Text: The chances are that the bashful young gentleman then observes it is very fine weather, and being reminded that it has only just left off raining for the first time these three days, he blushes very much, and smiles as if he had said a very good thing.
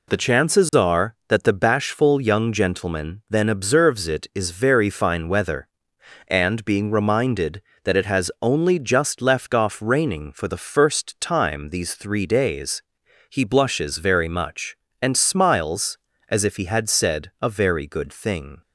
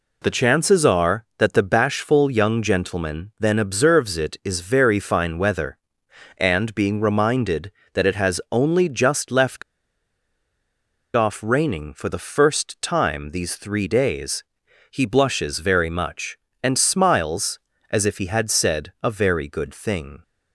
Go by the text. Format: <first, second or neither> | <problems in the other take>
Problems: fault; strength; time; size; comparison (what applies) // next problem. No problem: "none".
first | pauses between "left" and "off"; strong; at 9.6 s; 1.5 s long